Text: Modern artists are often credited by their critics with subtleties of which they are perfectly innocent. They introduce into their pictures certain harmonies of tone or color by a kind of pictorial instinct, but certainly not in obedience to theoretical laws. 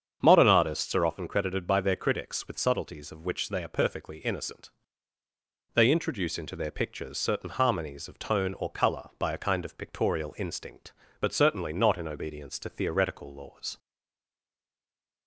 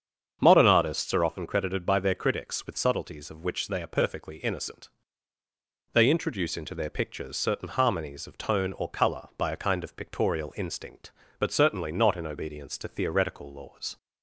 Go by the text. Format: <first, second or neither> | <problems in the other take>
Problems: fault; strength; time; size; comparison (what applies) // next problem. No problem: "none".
second | starts louder than the rest; strong; until 1.2 s; 7.5 dB; strong in the second // stays silent after the last word; noticeable; from 13.7 s on; 1.5 s long